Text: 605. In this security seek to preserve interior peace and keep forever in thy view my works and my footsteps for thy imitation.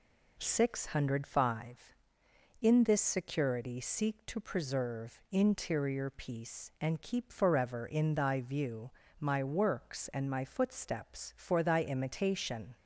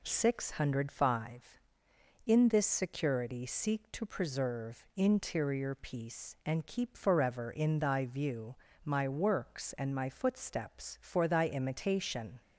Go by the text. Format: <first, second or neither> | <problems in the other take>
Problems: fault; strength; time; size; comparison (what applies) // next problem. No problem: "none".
neither | pauses between "view" and "my"; slight; the same in both